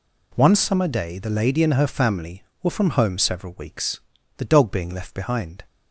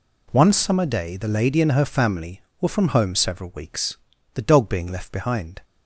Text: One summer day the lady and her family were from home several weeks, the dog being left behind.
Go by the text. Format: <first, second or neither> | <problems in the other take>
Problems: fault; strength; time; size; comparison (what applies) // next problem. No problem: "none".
neither | none